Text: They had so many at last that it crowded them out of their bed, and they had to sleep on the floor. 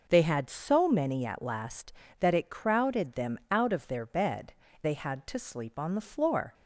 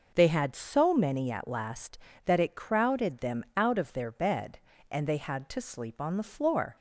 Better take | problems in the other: second | skips "and"; at 4.6 s

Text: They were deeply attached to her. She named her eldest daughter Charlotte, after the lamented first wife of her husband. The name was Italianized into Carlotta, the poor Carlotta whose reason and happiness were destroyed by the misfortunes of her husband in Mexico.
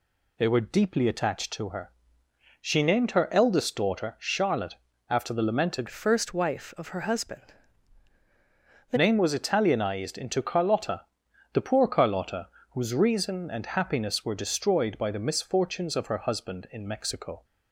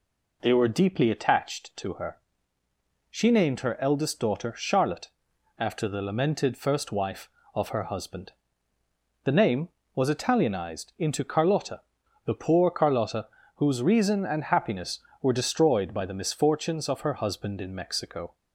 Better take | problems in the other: second | changes voice from "first" to "The"; from 5.8 to 8.9 s; 3.1 s long // pauses between "Carlotta" and "whose"; slight; at 12.4 s; 0.24 s long; slight in the second

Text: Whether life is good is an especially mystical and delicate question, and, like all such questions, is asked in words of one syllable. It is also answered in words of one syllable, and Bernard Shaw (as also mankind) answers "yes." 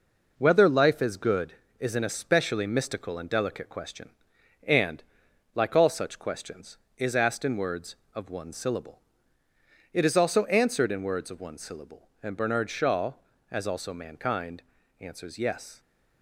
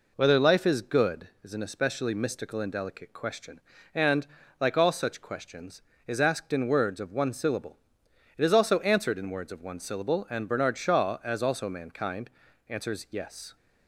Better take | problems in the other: second | gets quieter; noticeable; throughout; 5 dB

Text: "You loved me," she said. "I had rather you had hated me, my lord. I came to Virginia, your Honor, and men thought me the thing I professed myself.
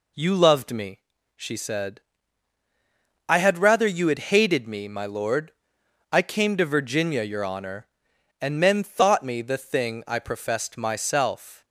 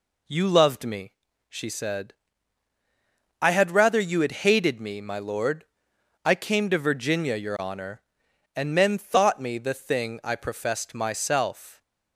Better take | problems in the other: neither | none

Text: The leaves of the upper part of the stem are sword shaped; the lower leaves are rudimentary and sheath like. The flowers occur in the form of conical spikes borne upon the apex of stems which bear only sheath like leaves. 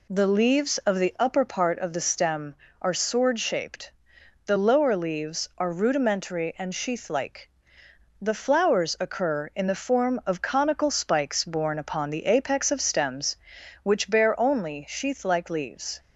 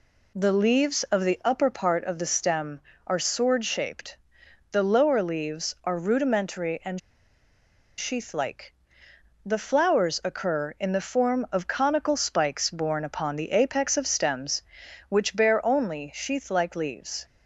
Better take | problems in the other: first | pauses between "and" and "sheath"; at 6.9 s; 0.98 s long

